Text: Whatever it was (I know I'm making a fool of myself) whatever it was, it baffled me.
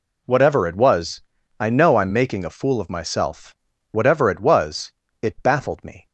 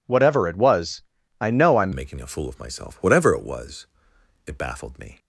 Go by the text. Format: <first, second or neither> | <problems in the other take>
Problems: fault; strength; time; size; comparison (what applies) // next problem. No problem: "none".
first | changes voice at "making"; from 1.9 s on; 3.2 s long